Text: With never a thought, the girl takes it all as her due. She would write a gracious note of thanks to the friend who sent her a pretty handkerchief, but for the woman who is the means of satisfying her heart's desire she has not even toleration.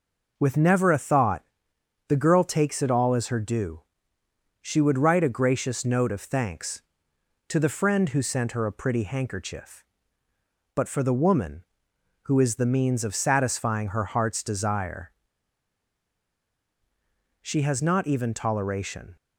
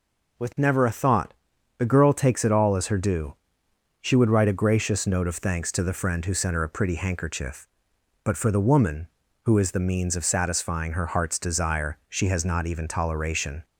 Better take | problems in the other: second | pauses between "desire" and "she"; strong; at 15.1 s; 2.3 s long

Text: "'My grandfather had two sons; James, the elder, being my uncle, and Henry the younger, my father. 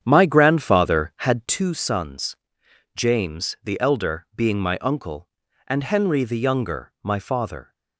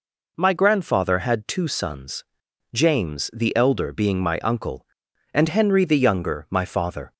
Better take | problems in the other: second | starts louder than the rest; strong; until 1.7 s; 8.5 dB

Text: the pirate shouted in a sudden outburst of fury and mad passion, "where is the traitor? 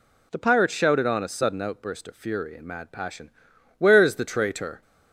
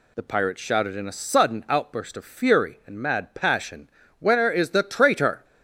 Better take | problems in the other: second | says "on" for "in"; at 1.0 s

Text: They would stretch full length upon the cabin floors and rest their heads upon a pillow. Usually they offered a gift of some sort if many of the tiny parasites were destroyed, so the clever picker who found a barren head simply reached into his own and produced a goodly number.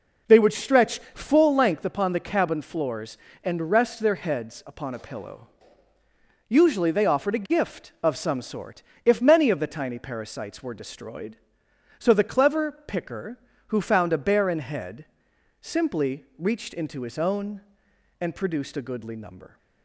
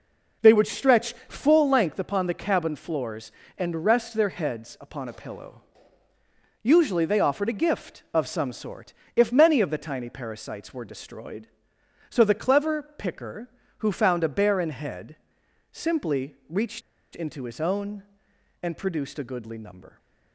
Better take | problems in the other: first | pauses between "stretch" and "full"; slight; at 1.1 s; 0.16 s long; slight in the first // pauses between "sort" and "if"; slight; at 8.9 s; 0.22 s long; slight in the first // pauses between "head" and "simply"; noticeable; at 15.1 s; 0.56 s long; noticeable in the first // pauses between "reached" and "into"; slight; at 16.8 s; 0.35 s long

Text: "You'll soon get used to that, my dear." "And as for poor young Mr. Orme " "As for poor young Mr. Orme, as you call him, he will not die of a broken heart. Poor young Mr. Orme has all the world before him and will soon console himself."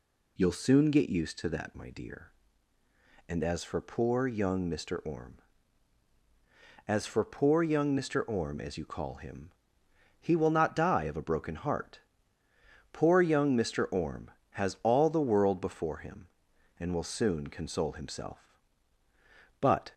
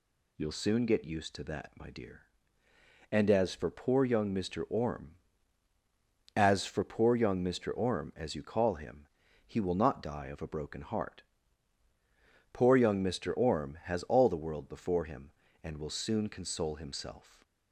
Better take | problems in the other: second | goes on to say "But"; slight; from 19.6 s on; 0.32 s long

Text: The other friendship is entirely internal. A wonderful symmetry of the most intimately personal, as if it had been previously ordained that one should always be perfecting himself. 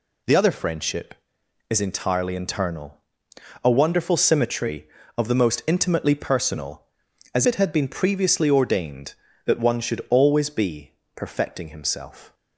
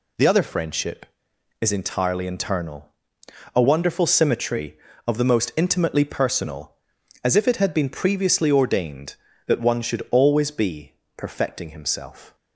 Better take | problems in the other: second | skips "if"; at 7.4 s // pauses between "be" and "perfecting"; slight; at 10.9 s; 0.24 s long; slight in the second

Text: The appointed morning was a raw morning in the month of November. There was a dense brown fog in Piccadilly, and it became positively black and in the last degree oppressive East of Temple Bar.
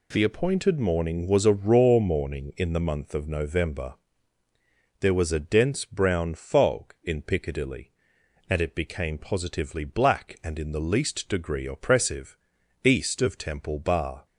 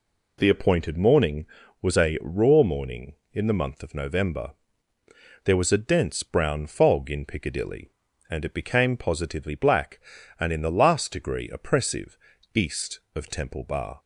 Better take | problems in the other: second | says "least" for "last"; at 10.8 s // pauses between "oppressive" and "East"; noticeable; at 12.3 s; 0.48 s long; slight in the second

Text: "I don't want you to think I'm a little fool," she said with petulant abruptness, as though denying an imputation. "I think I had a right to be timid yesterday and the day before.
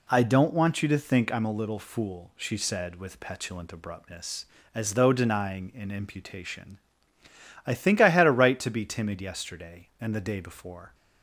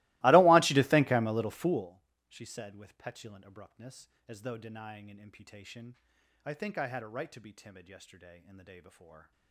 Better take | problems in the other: first | starts louder than the rest; strong; until 1.9 s; 22 dB

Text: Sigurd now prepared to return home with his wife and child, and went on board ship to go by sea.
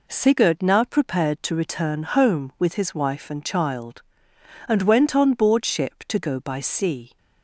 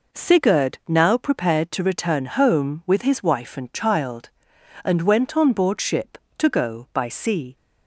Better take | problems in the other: neither | none

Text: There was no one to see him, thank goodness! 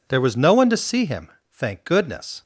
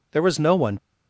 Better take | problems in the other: first | stops before "to see him thank goodness"; at 0.7 s

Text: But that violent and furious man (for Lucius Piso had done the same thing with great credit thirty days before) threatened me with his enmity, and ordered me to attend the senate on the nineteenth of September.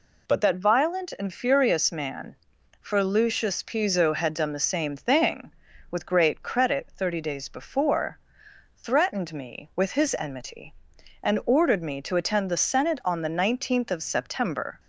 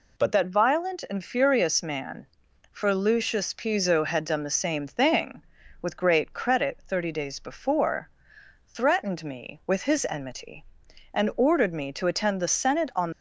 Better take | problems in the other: first | stops before "the nineteenth of September"; at 13.1 s

